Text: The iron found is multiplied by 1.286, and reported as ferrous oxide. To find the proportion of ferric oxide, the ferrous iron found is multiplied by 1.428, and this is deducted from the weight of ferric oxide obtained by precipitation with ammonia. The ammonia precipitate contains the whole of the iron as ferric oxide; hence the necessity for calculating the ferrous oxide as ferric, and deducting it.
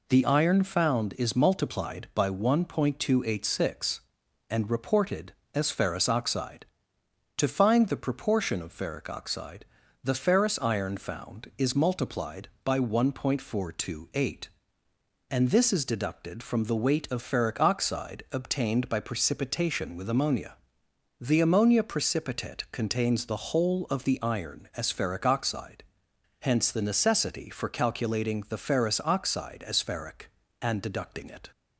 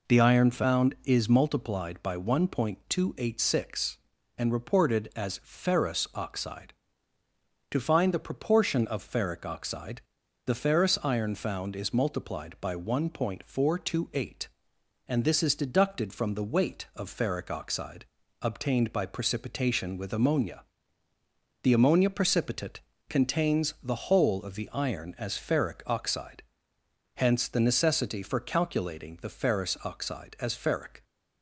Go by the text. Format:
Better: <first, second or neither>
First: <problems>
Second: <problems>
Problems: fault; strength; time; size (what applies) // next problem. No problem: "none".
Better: first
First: none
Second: pauses between "oxide" and "obtained"; slight; at 18.0 s; 0.36 s long // pauses between "precipitate" and "contains"; slight; at 22.8 s; 0.26 s long // stops before "and deducting it"; at 31.0 s